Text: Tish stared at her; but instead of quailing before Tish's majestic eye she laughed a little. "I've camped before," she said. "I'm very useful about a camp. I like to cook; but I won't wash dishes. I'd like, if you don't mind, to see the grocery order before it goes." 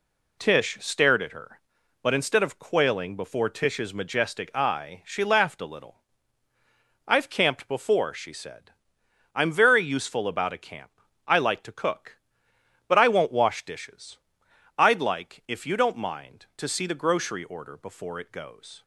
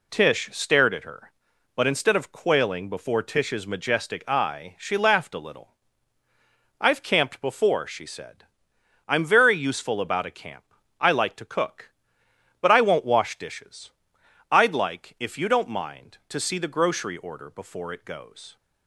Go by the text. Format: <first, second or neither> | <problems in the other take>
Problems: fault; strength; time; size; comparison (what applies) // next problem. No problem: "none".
neither | none